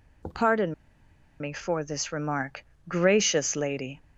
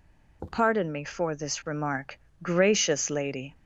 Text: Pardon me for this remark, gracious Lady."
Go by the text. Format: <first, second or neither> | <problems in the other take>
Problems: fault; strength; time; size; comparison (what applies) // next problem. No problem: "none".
second | pauses between "Pardon" and "me"; noticeable; at 0.7 s; 0.68 s long